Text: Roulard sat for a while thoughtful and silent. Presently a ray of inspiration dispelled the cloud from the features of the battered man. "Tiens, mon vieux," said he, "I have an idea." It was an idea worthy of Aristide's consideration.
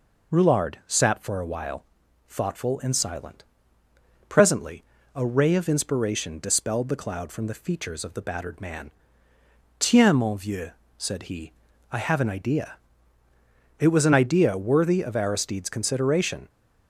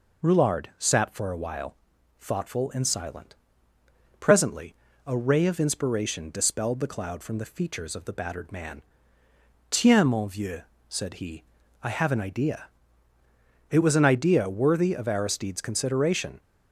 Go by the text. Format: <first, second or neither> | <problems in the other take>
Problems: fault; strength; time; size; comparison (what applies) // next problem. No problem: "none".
neither | pauses between "while" and "thoughtful"; the same in both // pauses between "Presently" and "a"; slight; the same in both